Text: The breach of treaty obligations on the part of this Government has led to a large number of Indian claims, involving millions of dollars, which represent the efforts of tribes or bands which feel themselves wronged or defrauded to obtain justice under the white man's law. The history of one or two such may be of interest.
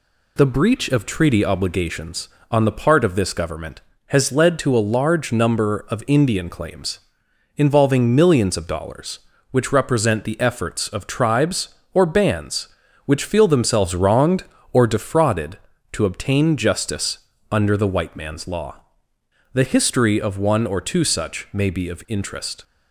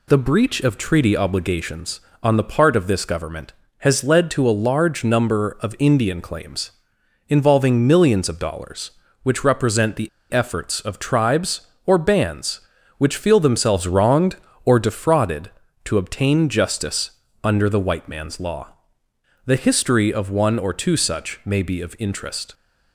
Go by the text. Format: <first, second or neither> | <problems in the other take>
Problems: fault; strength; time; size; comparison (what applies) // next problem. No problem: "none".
first | pauses between "the" and "efforts"; slight; at 10.0 s; 0.22 s long // pauses between "justice" and "under"; slight; at 17.0 s; 0.34 s long; slight in the first